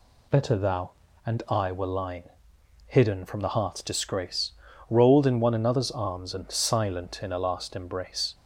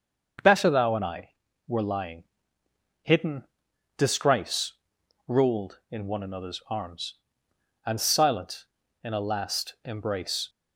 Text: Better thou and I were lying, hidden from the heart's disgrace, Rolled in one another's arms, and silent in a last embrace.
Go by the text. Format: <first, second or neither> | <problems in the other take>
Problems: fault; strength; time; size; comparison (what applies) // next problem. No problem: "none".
first | starts louder than the rest; until 1.7 s; 6.5 dB // skips "from the heart's"; at 3.7 s